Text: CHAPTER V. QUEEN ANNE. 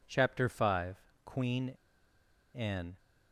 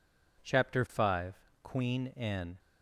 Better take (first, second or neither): second